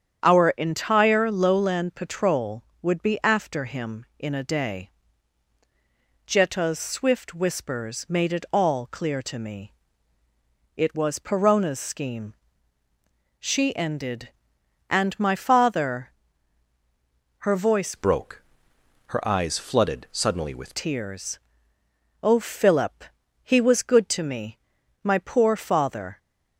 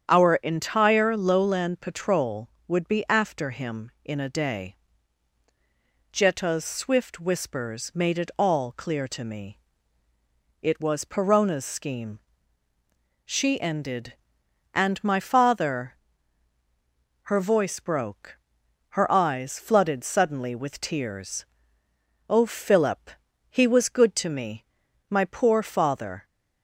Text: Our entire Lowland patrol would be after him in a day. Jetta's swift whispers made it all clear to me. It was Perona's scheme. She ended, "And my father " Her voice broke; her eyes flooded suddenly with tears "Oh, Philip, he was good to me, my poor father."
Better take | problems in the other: second | starts louder than the rest; strong; until 1.3 s; 8 dB; strong in the second // changes voice from "broke" to "with"; from 17.9 to 20.7 s; 2.8 s long // pauses between "tears" and "Oh"; noticeable; at 21.3 s; 0.82 s long; noticeable in the second

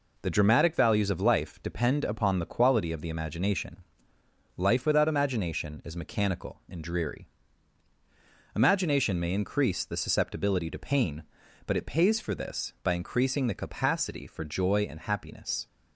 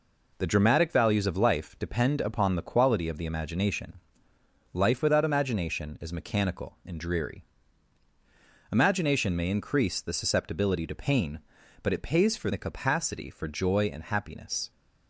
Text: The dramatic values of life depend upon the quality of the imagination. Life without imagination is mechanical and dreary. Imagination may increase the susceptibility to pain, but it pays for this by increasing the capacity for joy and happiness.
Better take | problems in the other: first | skips "this by increasing"; at 12.5 s

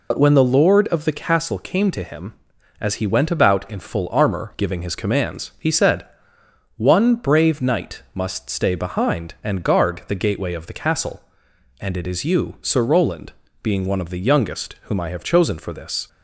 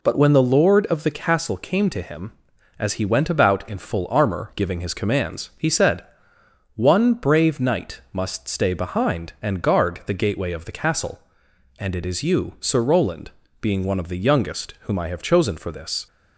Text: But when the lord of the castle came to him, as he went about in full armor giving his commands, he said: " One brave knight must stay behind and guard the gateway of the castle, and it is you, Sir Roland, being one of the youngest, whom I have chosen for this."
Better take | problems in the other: second | loses the start of "But"; at 0.1 s; 65 ms

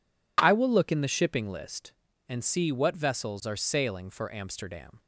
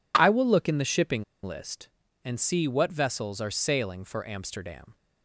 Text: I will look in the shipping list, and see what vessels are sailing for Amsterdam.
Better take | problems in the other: first | pauses between "shipping" and "list"; slight; at 1.2 s; 0.20 s long

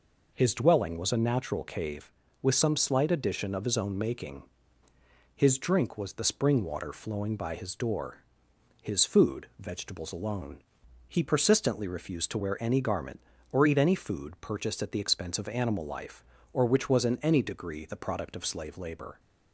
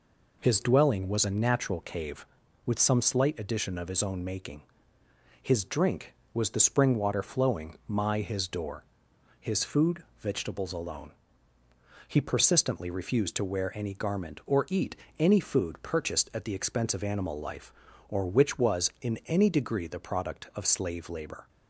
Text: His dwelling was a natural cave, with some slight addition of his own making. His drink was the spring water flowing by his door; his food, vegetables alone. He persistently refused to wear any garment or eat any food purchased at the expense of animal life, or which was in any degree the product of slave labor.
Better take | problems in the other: first | says "my" for "by"; at 7.8 s // pauses between "eat" and "any"; slight; at 14.9 s; 0.24 s long

